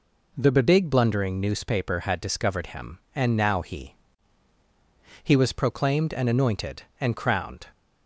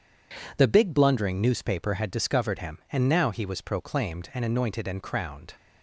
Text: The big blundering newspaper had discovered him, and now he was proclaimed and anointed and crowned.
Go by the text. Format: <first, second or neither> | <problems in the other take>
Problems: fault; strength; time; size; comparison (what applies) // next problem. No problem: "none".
second | says "he" twice; at 5.2 s